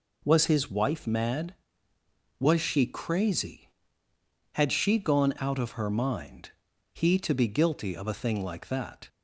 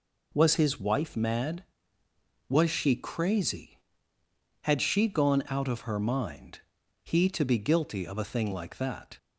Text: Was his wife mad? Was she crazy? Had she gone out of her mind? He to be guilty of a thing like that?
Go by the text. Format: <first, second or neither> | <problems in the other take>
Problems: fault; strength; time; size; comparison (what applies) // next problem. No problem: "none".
neither | none